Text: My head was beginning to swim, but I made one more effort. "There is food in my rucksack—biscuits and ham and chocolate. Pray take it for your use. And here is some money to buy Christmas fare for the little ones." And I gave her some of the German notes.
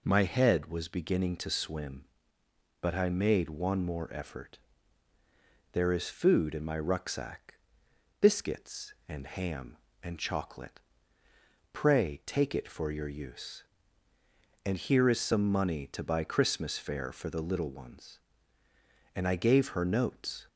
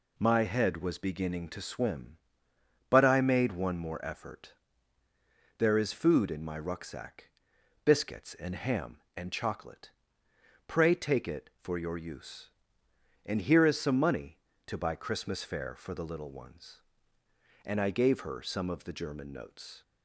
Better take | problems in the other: second | skips "some of the German"; at 19.8 s

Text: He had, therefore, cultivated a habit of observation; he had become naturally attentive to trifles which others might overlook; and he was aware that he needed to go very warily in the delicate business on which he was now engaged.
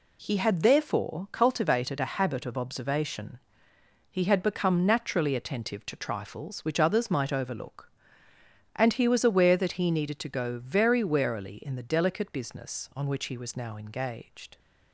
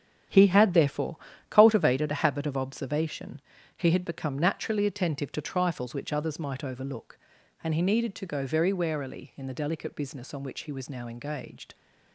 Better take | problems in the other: first | starts louder than the rest; strong; until 1.6 s; 9.5 dB // skips "was aware that he"; at 7.8 s

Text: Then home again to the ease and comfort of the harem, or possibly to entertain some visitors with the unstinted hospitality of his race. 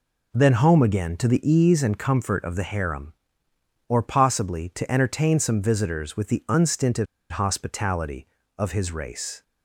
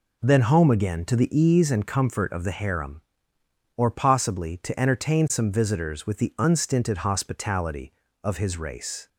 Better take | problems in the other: second | pauses between "unstinted" and "hospitality"; slight; at 7.0 s; 0.26 s long

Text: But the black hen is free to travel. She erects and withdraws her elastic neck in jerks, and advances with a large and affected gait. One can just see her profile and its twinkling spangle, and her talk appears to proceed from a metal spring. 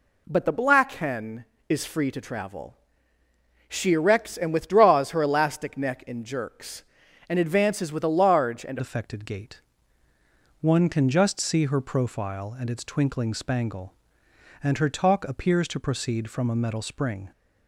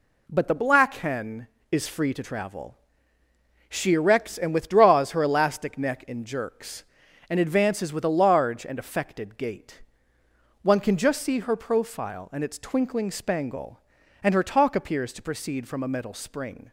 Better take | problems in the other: second | changes voice at "affected"; from 8.7 s on; 8.6 s long

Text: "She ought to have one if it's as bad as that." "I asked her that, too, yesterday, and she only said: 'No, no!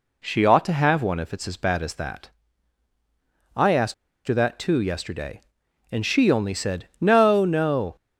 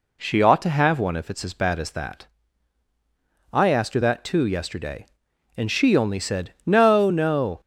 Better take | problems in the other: second | pauses between "asked" and "her"; slight; at 3.9 s; 0.33 s long

